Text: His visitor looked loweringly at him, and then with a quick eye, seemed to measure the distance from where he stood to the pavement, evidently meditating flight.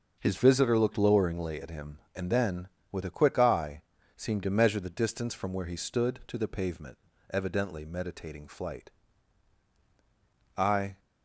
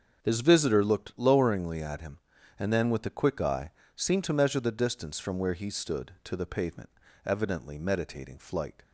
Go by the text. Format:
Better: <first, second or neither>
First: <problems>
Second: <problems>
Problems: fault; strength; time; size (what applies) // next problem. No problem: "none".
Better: second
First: starts louder than the rest; until 1.1 s; 6.5 dB // goes on to say "I"; slight; from 10.5 s on; 0.42 s long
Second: starts louder than the rest; until 1.2 s; 6.5 dB